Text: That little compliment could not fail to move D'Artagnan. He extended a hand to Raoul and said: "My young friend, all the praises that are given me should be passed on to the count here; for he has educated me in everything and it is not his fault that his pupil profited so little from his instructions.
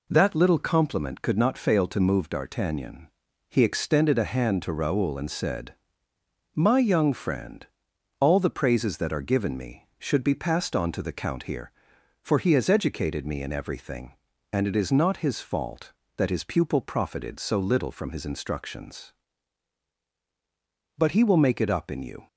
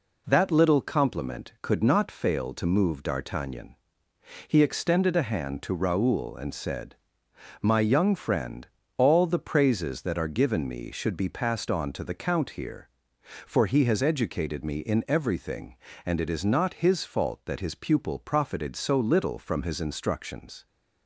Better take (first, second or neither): second